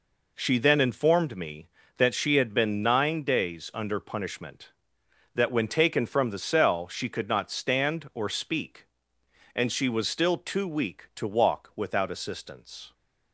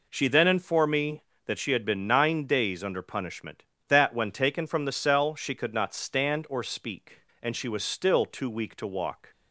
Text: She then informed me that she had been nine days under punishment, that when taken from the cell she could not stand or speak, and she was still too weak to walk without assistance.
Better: first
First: none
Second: stops before "without assistance"; at 9.3 s

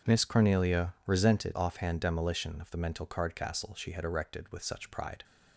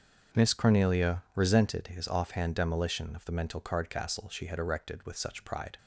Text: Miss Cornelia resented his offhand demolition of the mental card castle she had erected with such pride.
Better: second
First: starts louder than the rest; until 1.1 s; 6.5 dB // skips "his"; at 1.5 s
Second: starts louder than the rest; until 1.4 s; 7 dB

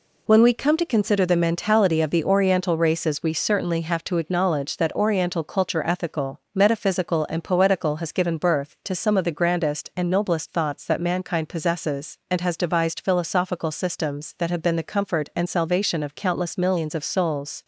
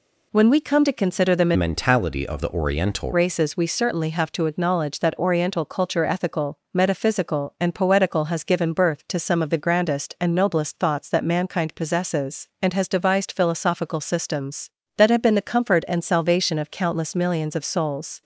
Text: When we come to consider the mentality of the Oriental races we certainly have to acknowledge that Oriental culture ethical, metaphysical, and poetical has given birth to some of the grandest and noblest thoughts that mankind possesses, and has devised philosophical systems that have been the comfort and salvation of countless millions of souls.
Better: first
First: none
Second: changes voice from "mentality" to "Oriental"; from 1.5 to 3.1 s; 1.6 s long

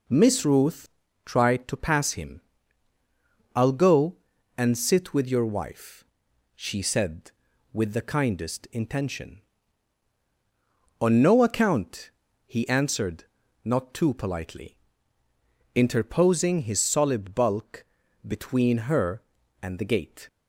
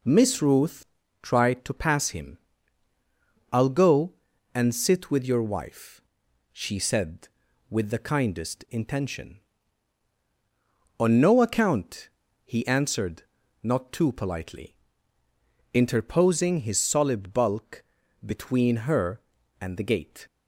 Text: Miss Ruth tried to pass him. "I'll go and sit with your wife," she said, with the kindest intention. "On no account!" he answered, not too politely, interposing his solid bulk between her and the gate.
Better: neither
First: pauses between "Ruth" and "tried"; slight; at 0.8 s; 0.34 s long // pauses between "bulk" and "between"; at 17.8 s; 0.42 s long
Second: pauses between "Ruth" and "tried"; slight; at 0.8 s; 0.34 s long // pauses between "bulk" and "between"; at 17.8 s; 0.42 s long

